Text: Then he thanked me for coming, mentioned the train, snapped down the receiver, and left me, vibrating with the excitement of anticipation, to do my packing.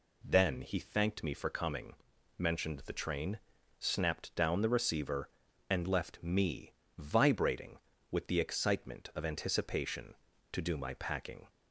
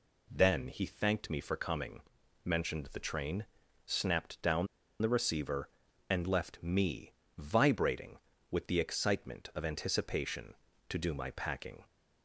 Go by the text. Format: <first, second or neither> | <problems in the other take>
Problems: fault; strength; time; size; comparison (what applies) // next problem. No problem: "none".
first | pauses between "down" and "the"; slight; at 4.6 s; 0.35 s long